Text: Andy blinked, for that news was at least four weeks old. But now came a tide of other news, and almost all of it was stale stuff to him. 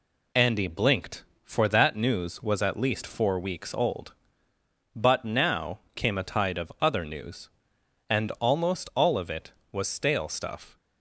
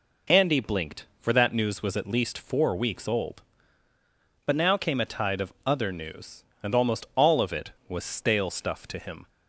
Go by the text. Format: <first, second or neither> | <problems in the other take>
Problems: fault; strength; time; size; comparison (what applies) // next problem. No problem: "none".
second | pauses between "now" and "came"; slight; at 5.7 s; 0.16 s long // stops before "to him"; at 10.7 s